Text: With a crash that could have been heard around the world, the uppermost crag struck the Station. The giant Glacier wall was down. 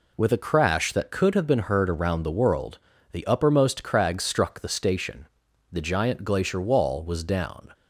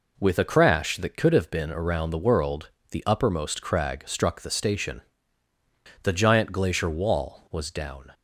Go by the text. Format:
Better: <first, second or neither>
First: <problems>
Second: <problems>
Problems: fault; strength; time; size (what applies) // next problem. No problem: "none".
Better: first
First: none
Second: skips "heard"; at 1.7 s